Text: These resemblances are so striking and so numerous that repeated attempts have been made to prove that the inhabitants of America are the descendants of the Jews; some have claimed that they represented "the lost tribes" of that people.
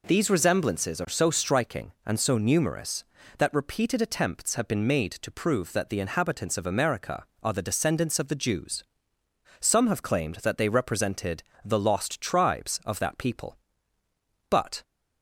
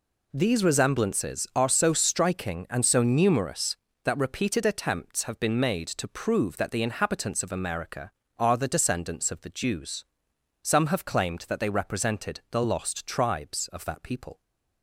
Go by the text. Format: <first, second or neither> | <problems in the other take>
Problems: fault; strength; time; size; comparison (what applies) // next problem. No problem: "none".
second | pauses between "represented" and "the"; slight; at 11.4 s; 0.22 s long // goes on to say "But"; slight; from 14.4 s on; 0.34 s long